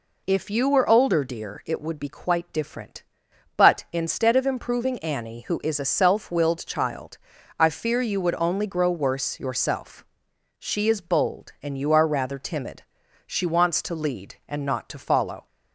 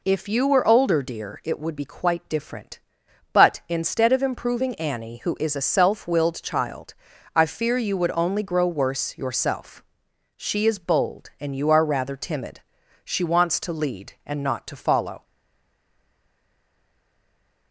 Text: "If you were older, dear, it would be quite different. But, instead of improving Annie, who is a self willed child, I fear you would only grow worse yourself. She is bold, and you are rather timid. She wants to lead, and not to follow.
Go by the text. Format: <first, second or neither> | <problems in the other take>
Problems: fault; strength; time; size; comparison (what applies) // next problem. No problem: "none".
first | stays silent after the last word; from 15.2 s on; 2.5 s long